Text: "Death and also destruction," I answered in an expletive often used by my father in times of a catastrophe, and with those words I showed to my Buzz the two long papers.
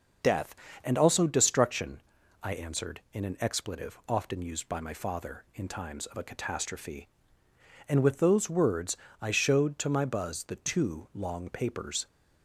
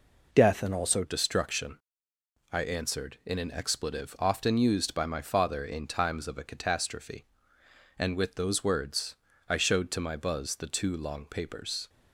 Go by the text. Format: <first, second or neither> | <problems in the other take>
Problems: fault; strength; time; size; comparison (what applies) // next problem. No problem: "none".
first | changes voice at "destruction"; from 1.0 s on; 10.8 s long // pauses between "words" and "I"; slight; at 9.1 s; 0.34 s long; slight in the first